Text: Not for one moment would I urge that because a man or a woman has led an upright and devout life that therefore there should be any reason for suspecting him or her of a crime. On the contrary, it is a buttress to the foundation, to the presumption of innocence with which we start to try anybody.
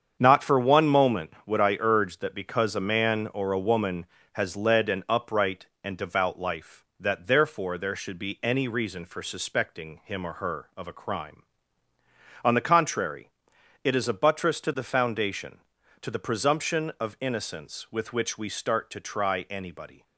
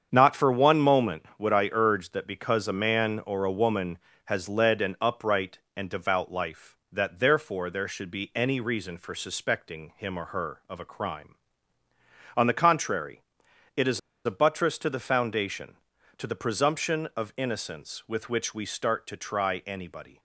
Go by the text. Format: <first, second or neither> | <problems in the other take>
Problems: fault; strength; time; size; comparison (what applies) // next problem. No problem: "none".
first | starts louder than the rest; strong; until 1.1 s; 7.5 dB; strong in the first // pauses between "is" and "a"; slight; at 13.9 s; 0.25 s long